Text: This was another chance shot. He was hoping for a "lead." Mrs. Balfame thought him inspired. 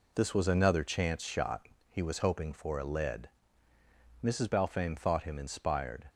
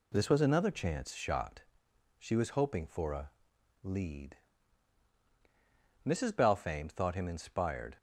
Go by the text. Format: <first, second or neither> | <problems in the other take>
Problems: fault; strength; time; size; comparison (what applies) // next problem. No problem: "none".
first | says "She" for "He"; at 2.1 s // pauses between "a" and "lead"; noticeable; at 3.2 s; 0.52 s long